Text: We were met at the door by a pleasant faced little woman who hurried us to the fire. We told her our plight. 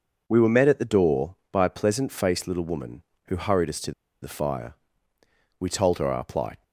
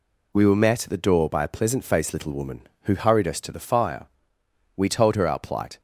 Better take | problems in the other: second | pauses between "to" and "the"; slight; at 3.9 s; 0.30 s long

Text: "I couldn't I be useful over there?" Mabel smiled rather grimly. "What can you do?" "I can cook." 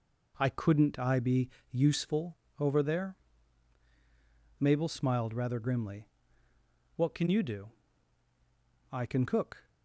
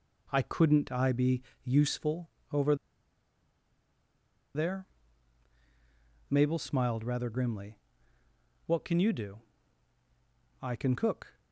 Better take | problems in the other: first | pauses between "be" and "useful"; slight; at 1.4 s; 0.24 s long; slight in the first // pauses between "useful" and "over"; slight; at 2.2 s; 0.24 s long; slight in the first // pauses between "over" and "there"; strong; at 2.7 s; 1.8 s long

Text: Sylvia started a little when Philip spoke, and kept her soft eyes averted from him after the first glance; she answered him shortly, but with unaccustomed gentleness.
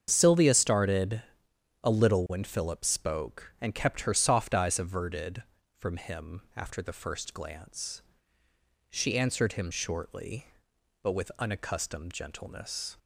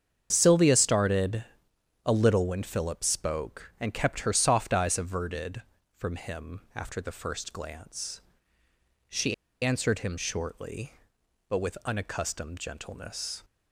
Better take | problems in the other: first | starts louder than the rest; strong; until 1.3 s; 7.5 dB; strong in the first // pauses between "started" and "a"; noticeable; at 1.4 s; 0.62 s long; noticeable in the first // pauses between "she" and "answered"; slight; at 9.3 s; 0.29 s long

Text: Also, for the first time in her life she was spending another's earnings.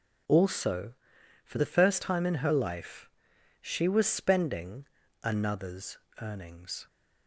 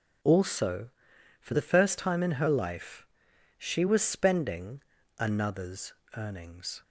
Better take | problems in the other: neither | pauses between "life" and "she"; noticeable; the same in both // pauses between "spending" and "another's"; slight; the same in both // pauses between "another's" and "earnings"; slight; the same in both

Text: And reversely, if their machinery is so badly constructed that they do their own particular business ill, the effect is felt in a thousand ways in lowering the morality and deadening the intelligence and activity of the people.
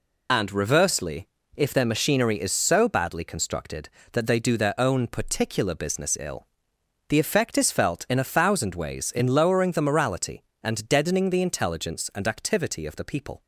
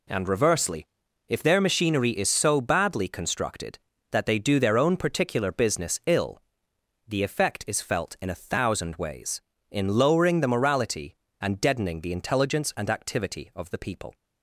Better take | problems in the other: second | loses the start of "And"; at 0.2 s; 45 ms

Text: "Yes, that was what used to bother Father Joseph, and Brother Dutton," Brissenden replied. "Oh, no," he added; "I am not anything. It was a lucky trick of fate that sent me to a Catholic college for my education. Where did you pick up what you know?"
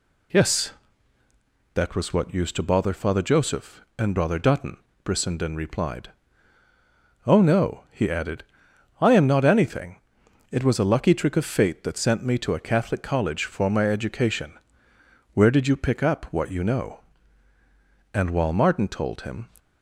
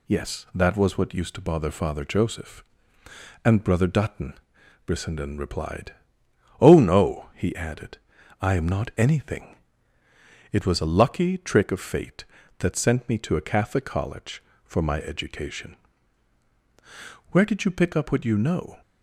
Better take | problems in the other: second | goes on to say "And while Martin told him"; from 18.1 s on; 1.3 s long

